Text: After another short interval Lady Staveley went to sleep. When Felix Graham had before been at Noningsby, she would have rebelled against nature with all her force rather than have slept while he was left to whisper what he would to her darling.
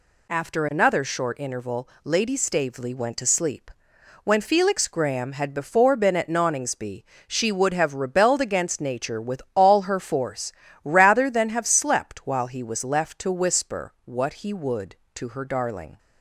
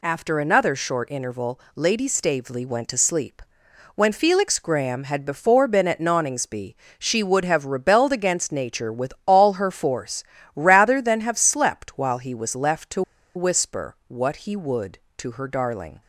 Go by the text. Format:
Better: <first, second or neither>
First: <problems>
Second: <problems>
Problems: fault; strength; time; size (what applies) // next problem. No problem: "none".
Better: first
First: pauses between "interval" and "Lady"; slight; at 1.8 s; 0.16 s long // pauses between "force" and "rather"; slight; at 10.5 s; 0.32 s long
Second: pauses between "interval" and "Lady"; slight; at 1.5 s; 0.16 s long // pauses between "force" and "rather"; slight; at 10.2 s; 0.32 s long // pauses between "to" and "whisper"; slight; at 13.0 s; 0.34 s long